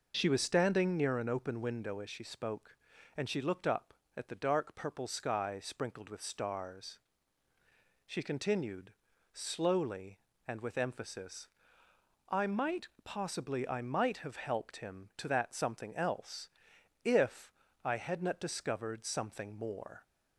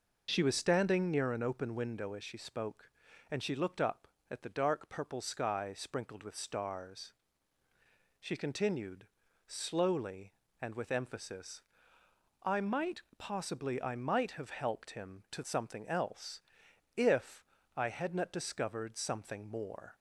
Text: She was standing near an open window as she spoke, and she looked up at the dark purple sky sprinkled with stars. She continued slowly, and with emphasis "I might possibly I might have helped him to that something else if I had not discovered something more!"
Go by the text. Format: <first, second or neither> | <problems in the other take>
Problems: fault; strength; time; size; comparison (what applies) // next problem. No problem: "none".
first | pauses between "continued" and "slowly"; at 9.0 s; 0.40 s long; also in the first // pauses between "emphasis" and "I"; noticeable; at 11.6 s; 0.80 s long; noticeable in the first // pauses between "might" and "possibly"; slight; at 13.0 s; 0.16 s long; slight in the first // skips "that"; at 15.4 s // pauses between "else" and "if"; noticeable; at 16.3 s; 0.56 s long; noticeable in the first // pauses between "if" and "I"; slight; at 17.4 s; 0.32 s long; slight in the first